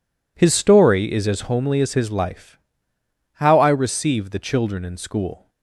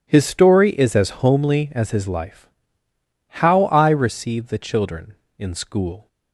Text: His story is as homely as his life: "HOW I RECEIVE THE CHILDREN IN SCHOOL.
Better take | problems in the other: neither | none

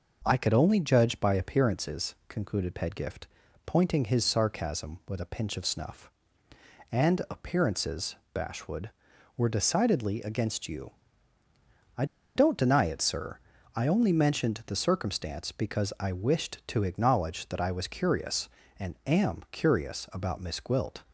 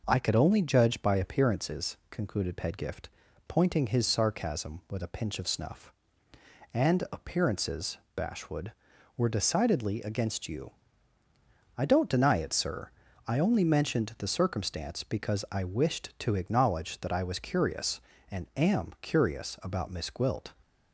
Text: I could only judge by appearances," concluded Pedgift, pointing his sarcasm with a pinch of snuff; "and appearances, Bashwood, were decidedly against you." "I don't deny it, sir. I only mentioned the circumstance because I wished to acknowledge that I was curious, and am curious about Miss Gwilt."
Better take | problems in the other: second | pauses between "I" and "don't"; slight; at 12.0 s; 0.30 s long

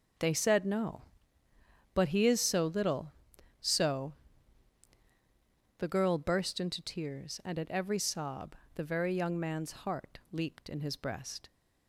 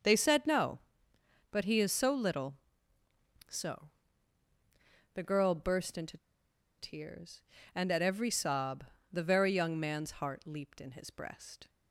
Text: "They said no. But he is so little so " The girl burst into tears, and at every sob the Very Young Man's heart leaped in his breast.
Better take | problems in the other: first | pauses between "into" and "tears"; noticeable; at 6.1 s; 0.62 s long // pauses between "sob" and "the"; slight; at 8.8 s; 0.26 s long; slight in the first

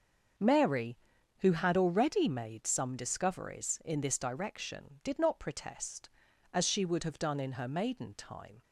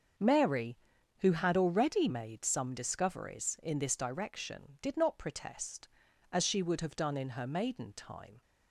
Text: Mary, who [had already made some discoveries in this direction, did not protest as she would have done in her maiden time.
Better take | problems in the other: neither | starts louder than the rest; the same in both

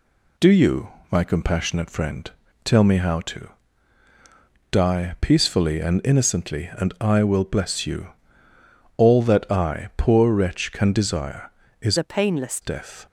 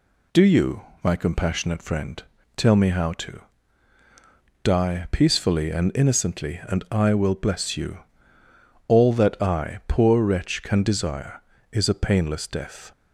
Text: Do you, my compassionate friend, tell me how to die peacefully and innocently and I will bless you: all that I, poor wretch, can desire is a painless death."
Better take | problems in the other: second | pauses between "to" and "die"; at 3.4 s; 1.2 s long; also in the second // changes voice from "a" to "painless"; from 11.9 to 12.6 s; 0.7 s long

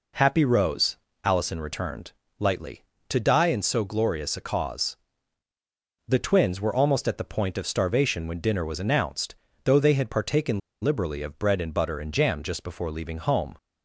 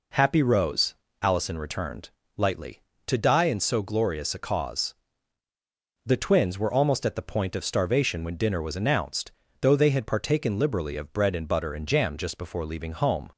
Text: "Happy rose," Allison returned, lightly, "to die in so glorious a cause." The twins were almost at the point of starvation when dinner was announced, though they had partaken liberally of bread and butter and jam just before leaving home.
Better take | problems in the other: second | pauses between "partaken" and "liberally"; slight; at 10.6 s; 0.23 s long

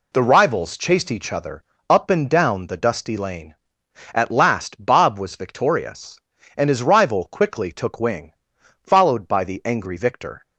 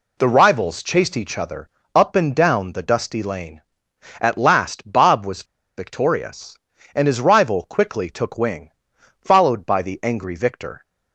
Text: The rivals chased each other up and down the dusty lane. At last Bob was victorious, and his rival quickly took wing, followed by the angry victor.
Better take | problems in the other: first | pauses between "other" and "up"; slight; at 1.6 s; 0.26 s long; slight in the first // pauses between "was" and "victorious"; slight; at 5.4 s; 0.31 s long

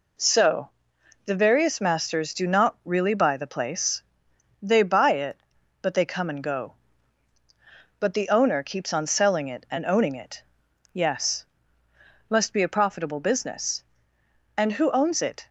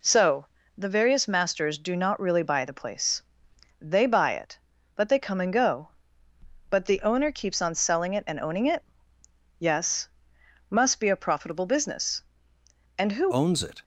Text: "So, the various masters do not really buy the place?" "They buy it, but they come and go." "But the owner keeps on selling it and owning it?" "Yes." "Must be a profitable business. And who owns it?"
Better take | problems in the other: first | changes voice at "owns"; from 13.3 s on; 0.5 s long

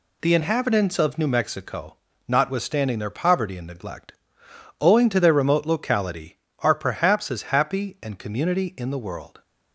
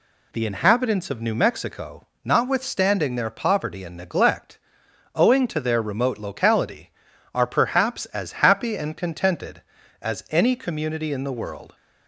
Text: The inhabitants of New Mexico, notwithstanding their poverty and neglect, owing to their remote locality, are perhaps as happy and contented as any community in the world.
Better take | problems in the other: second | skips "contented as any"; at 8.1 s

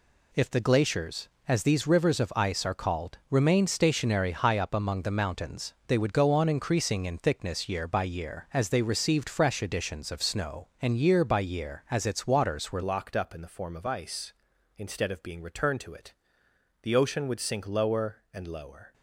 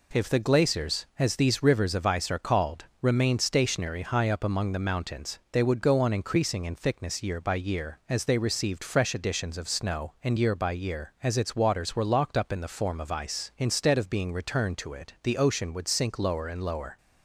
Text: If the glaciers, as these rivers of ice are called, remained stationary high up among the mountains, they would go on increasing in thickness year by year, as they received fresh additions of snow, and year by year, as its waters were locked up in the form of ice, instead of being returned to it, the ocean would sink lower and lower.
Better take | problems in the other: second | changes voice at "locked"; from 12.8 s on; 6.1 s long

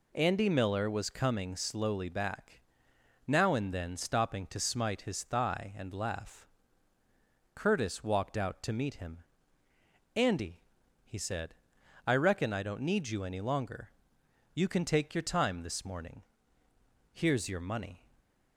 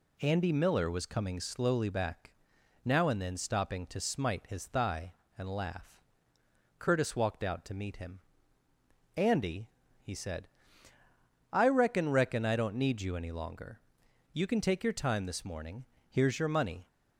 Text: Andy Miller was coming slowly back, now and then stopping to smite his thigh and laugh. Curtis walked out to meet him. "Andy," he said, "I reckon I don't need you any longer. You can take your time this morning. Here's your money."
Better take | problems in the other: first | says "reckon" twice; at 12.0 s

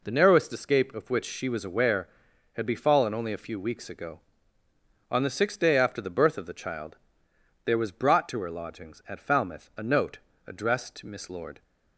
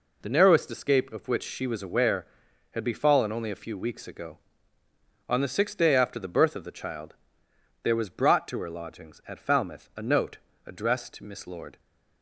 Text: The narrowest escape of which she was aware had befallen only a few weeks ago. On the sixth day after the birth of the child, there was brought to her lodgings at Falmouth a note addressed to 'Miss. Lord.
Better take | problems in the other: neither | pauses between "note" and "addressed"; slight; the same in both

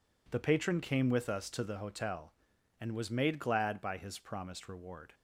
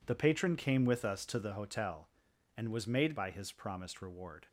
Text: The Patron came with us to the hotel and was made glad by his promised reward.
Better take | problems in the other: first | skips "glad"; at 3.1 s

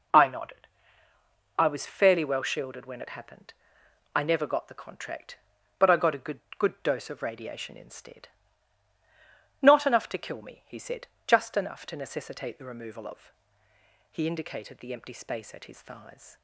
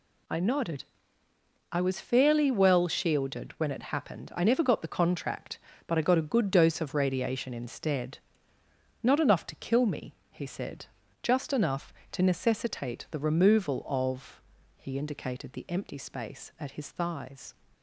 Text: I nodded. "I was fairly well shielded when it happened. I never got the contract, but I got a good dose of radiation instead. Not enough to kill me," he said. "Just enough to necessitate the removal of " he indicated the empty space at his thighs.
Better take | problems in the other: second | says "good" twice; at 6.5 s

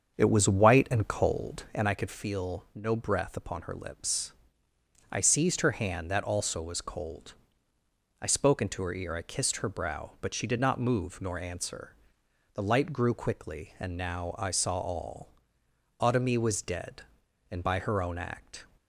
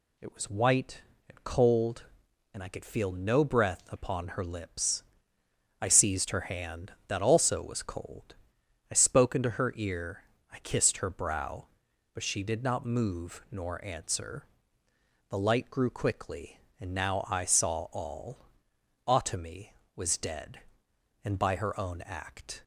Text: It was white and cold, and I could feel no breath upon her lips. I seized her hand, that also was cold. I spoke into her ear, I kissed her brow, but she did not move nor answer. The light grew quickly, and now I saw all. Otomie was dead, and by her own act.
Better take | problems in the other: second | starts louder than the rest; until 1.9 s; 7 dB

